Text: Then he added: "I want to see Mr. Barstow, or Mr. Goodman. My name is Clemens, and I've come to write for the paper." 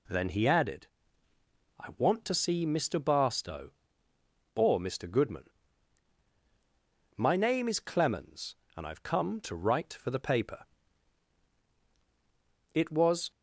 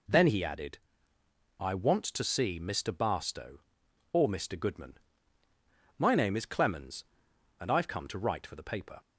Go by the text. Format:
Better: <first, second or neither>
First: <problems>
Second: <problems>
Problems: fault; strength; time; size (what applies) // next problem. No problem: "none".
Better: second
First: goes on to say "It was"; from 12.7 s on; 0.58 s long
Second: none